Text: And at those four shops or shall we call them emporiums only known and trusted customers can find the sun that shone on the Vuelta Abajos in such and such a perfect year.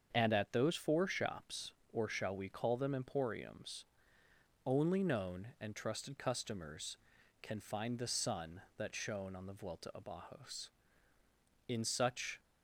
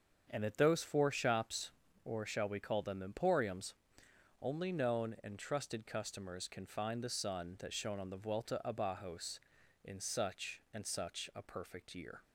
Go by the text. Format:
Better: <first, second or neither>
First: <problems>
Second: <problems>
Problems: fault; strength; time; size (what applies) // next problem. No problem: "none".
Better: second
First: starts louder than the rest; until 1.1 s; 7 dB // pauses between "emporiums" and "only"; noticeable; at 3.8 s; 0.80 s long // stops before "and such a perfect year"; at 12.3 s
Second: starts louder than the rest; until 1.3 s; 7 dB // pauses between "emporiums" and "only"; noticeable; at 3.7 s; 0.66 s long